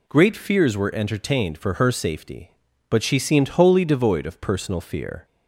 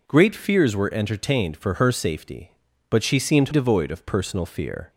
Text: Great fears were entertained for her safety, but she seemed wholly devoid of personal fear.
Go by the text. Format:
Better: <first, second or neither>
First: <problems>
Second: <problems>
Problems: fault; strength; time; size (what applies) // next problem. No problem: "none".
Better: first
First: none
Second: skips "wholly"; at 3.4 s